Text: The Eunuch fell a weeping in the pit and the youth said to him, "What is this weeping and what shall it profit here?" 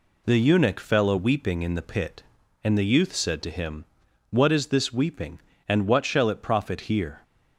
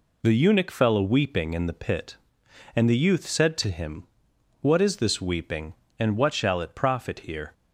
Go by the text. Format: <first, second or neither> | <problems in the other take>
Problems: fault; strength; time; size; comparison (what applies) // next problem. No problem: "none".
neither | none